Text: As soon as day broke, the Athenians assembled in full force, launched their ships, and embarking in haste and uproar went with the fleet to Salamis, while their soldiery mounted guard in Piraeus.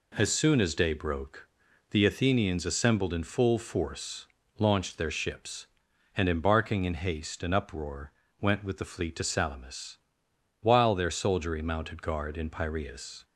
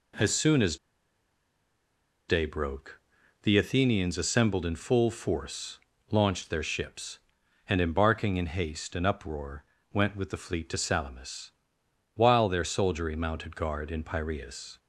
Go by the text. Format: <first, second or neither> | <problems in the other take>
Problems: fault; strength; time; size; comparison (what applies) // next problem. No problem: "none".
first | pauses between "as" and "day"; strong; at 0.7 s; 1.5 s long // pauses between "uproar" and "went"; slight; at 9.6 s; 0.26 s long; slight in the first